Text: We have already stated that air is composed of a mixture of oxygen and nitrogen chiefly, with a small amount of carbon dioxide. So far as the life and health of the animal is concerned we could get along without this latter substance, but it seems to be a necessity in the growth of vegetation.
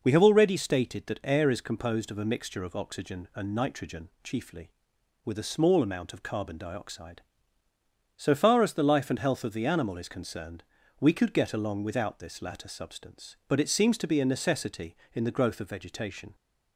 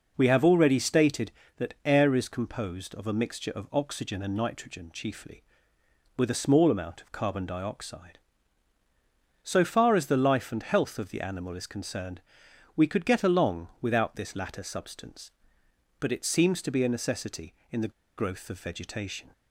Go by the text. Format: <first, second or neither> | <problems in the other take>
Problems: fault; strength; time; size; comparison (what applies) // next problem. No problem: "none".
first | pauses between "concerned" and "we"; noticeable; at 12.2 s; 0.56 s long; also in the first // pauses between "the" and "growth"; slight; at 17.9 s; 0.26 s long